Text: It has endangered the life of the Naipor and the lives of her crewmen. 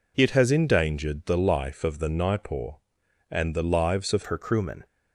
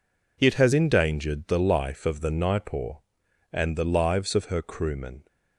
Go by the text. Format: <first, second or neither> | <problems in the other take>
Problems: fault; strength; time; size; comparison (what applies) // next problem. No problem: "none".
second | changes voice at "her"; from 4.2 s on; 0.6 s long